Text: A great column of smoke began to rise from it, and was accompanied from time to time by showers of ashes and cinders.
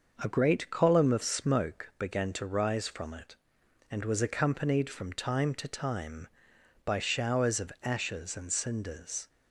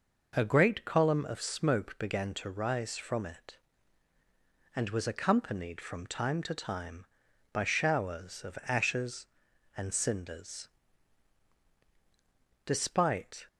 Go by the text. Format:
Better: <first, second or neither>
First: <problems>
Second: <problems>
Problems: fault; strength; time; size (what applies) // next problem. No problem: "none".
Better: first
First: none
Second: goes on to say "Despite"; noticeable; from 12.6 s on; 0.80 s long